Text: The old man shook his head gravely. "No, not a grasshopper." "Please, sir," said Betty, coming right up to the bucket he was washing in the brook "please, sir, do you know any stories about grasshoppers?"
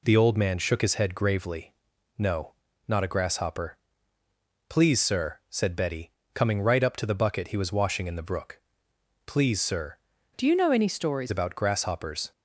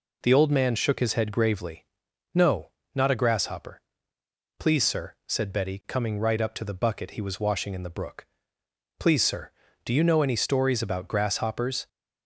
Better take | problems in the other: second | pauses between "brook" and "please"; noticeable; at 8.6 s; 0.64 s long; noticeable in the second // changes voice from "do" to "stories"; from 10.3 to 11.3 s; 1.0 s long

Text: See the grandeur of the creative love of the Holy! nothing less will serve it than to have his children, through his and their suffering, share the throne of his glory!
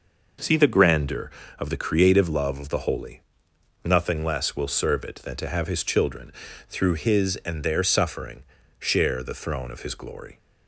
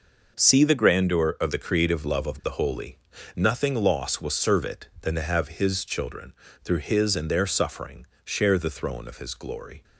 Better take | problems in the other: first | says "loss" for "less"; at 3.7 s

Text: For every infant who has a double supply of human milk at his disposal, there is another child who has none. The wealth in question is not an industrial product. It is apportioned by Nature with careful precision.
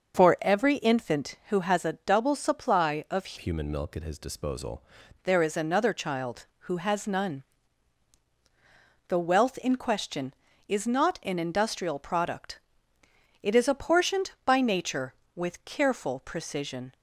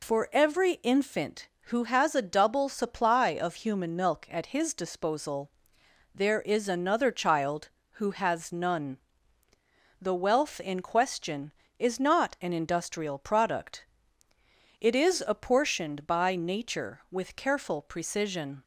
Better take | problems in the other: second | changes voice from "human" to "disposal"; from 3.3 to 4.8 s; 1.5 s long

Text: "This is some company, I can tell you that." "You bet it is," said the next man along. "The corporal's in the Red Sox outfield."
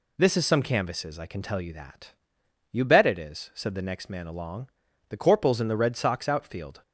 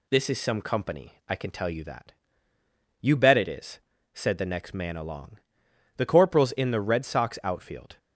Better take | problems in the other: second | says "canvases" for "company"; at 0.6 s

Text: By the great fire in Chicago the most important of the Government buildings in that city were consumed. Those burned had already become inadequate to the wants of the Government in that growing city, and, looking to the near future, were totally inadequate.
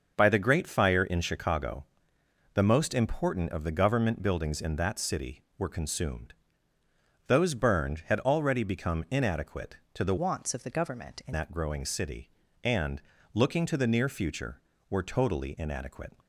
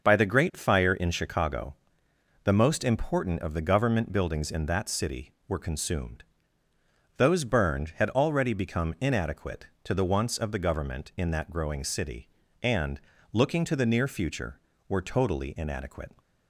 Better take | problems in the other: second | starts louder than the rest; until 1.1 s; 6.5 dB; also in the second // pauses between "Chicago" and "the"; noticeable; at 1.8 s; 0.68 s long; noticeable in the second // changes voice from "wants" to "in"; from 10.1 to 11.3 s; 1.2 s long

